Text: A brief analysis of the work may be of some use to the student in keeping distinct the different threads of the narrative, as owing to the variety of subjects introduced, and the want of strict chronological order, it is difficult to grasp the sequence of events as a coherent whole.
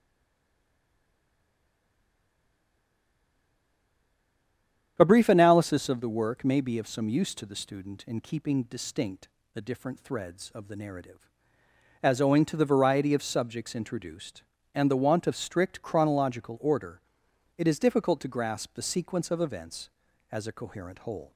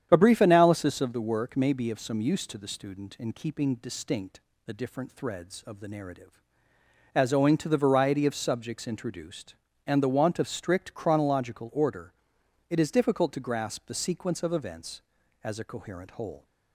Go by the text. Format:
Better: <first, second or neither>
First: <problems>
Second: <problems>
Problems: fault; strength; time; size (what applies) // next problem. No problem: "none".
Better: second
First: stays silent before the first word; strong; until 4.9 s; 4.9 s long // starts louder than the rest; strong; until 5.9 s; 9 dB // pauses between "distinct" and "the"; slight; at 9.2 s; 0.26 s long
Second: starts louder than the rest; strong; until 1.1 s; 9 dB // pauses between "distinct" and "the"; slight; at 4.4 s; 0.26 s long